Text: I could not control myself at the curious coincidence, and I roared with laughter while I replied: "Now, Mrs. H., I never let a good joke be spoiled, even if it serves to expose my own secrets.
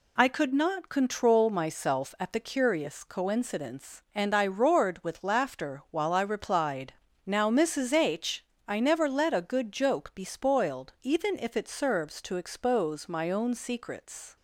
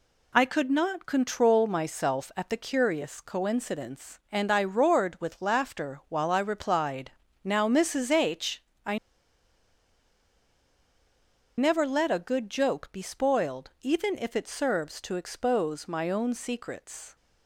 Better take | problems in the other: first | pauses between "I" and "never"; strong; at 8.9 s; 2.6 s long

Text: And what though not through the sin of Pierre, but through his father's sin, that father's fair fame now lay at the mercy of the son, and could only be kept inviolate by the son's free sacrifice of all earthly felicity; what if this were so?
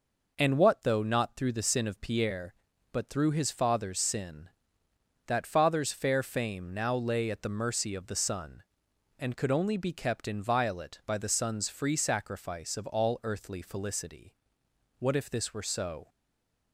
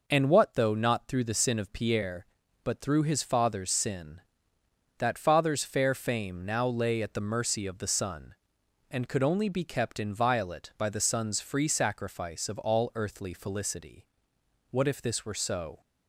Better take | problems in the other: second | stays silent after the last word; slight; from 16.0 s on; 0.7 s long

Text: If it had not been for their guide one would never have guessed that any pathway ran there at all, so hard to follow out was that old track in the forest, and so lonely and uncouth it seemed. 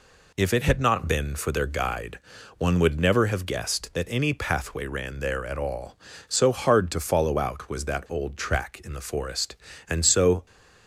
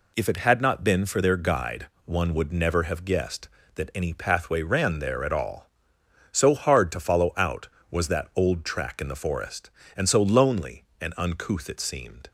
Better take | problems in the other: second | pauses between "guide" and "one"; at 2.1 s; 0.38 s long; slight in the second // stops before "lonely and uncouth it seemed"; at 10.4 s

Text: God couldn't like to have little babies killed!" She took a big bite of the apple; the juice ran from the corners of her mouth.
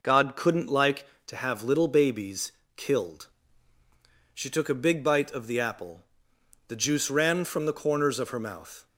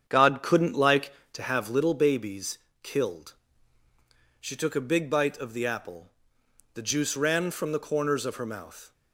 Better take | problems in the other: first | starts louder than the rest; strong; until 1.9 s; 8 dB // pauses between "babies" and "killed"; slight; at 2.5 s; 0.24 s long; slight in the first

